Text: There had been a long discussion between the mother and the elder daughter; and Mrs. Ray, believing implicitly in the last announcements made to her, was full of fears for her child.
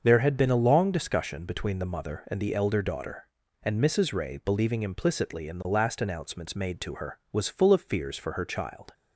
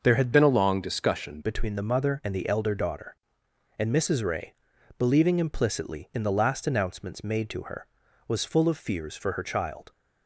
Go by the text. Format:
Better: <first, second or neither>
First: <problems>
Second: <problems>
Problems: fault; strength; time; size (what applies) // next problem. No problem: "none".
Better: first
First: starts louder than the rest; until 1.0 s; 6.5 dB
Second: starts louder than the rest; noticeable; until 1.0 s; 6 dB // changes voice from "been" to "discussion"; from 0.3 to 1.4 s; 1.1 s long